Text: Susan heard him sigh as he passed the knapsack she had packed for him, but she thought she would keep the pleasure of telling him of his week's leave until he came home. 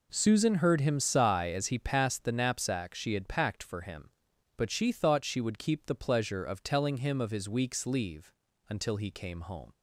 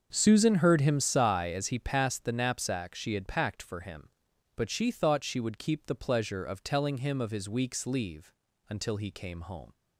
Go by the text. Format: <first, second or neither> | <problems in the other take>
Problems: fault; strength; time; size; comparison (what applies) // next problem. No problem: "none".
first | starts louder than the rest; until 1.2 s; 6.5 dB // pauses between "leave" and "until"; slight; at 8.3 s; 0.34 s long; slight in the first